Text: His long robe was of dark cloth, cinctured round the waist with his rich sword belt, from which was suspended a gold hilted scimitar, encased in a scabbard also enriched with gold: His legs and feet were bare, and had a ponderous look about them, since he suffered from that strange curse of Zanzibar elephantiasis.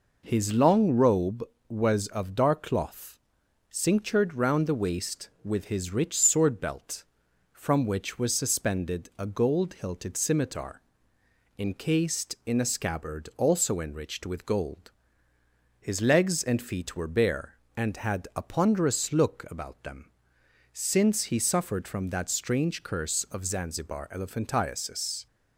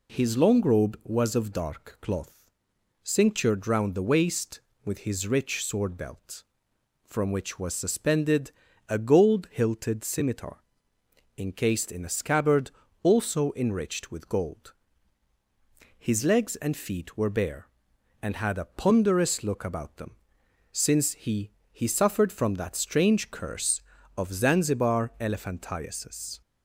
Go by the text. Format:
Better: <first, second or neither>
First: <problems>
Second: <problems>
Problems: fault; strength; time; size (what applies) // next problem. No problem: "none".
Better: first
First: none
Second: pauses between "suspended" and "a"; at 8.5 s; 0.38 s long // pauses between "scabbard" and "also"; slight; at 12.7 s; 0.32 s long // says "he" twice; at 21.7 s